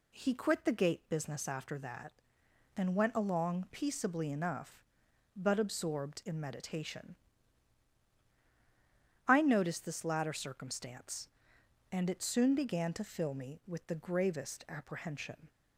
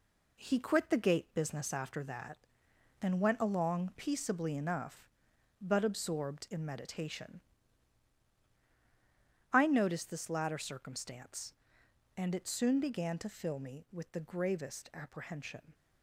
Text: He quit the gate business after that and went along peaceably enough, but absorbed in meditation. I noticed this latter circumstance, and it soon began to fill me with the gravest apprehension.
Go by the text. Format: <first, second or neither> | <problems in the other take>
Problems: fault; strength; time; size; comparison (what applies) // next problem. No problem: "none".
first | gets quieter; throughout; 6.5 dB